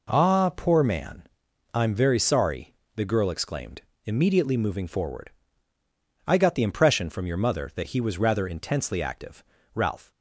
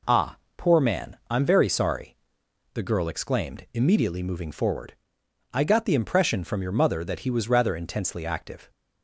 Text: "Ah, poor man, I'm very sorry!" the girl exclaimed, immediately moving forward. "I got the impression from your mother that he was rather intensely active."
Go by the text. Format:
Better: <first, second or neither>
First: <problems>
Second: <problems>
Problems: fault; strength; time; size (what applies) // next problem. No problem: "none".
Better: second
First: goes on to say "Ralph"; slight; from 9.7 s on; 0.36 s long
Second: none